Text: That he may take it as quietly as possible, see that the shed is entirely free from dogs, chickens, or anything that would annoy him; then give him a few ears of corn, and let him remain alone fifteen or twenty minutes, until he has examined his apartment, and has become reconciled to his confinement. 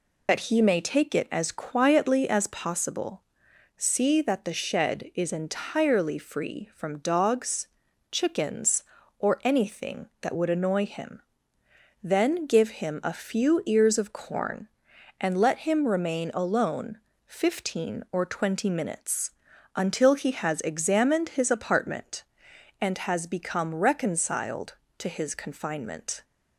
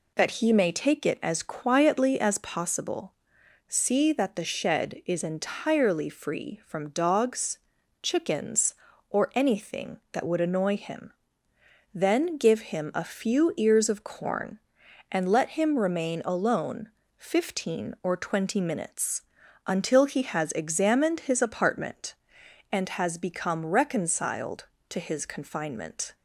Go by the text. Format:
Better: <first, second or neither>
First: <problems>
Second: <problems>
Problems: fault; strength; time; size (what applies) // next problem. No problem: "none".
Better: second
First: loses the start of "That"; at 0.2 s; 50 ms // pauses between "alone" and "fifteen"; slight; at 16.9 s; 0.28 s long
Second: pauses between "alone" and "fifteen"; slight; at 16.8 s; 0.28 s long